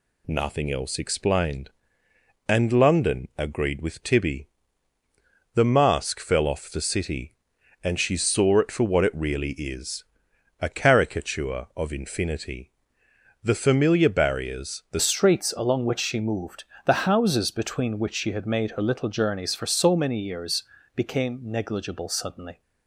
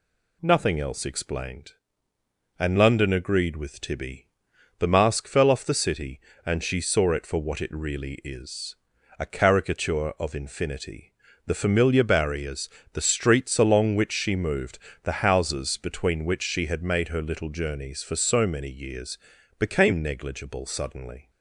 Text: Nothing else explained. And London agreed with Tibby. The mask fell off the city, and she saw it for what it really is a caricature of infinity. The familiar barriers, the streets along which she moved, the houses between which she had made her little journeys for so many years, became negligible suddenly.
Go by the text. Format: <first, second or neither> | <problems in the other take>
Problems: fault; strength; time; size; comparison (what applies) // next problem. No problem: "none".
second | pauses between "is" and "a"; noticeable; at 10.0 s; 0.58 s long; also in the second // changes voice at "streets"; from 14.9 s on; 7.7 s long